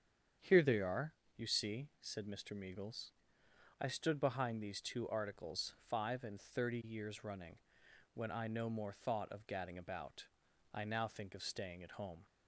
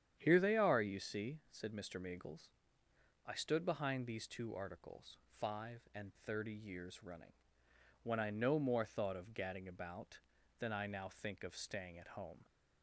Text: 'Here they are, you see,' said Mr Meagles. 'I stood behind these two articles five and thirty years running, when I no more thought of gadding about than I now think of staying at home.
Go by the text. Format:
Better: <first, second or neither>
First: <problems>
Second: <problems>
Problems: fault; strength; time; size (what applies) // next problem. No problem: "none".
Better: second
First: starts louder than the rest; strong; until 1.6 s; 8 dB // skips "than"; at 10.4 s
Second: starts louder than the rest; strong; until 1.2 s; 9 dB